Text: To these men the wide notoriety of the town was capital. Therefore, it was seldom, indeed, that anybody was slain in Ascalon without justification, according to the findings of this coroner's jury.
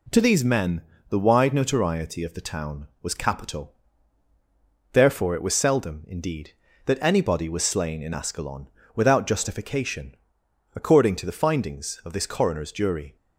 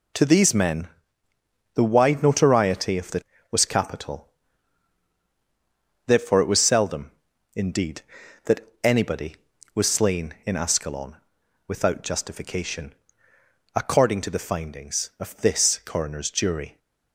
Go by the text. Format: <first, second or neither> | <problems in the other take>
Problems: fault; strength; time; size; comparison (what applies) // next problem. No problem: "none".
first | pauses between "men" and "the"; noticeable; at 0.8 s; 0.88 s long; slight in the first // skips "town"; at 3.3 s // pauses between "that" and "anybody"; slight; at 8.6 s; 0.16 s long // pauses between "Ascalon" and "without"; noticeable; at 11.1 s; 0.50 s long; slight in the first